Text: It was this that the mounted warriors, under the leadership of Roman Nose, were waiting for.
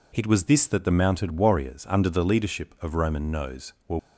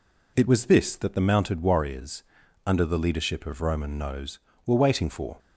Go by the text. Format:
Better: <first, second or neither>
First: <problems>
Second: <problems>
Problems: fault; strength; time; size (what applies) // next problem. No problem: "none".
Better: second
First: stops before "waiting for"; at 3.9 s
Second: none